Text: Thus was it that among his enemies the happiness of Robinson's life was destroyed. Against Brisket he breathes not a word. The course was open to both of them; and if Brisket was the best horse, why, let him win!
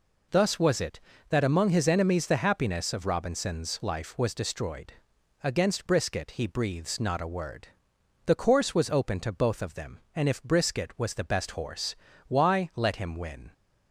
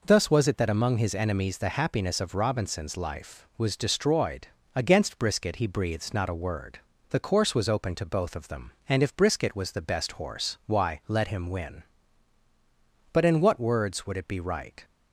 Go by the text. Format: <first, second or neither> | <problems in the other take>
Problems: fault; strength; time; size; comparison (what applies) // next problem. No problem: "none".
first | goes on to say "But in what words would it be right"; strong; from 13.1 s on; 1.7 s long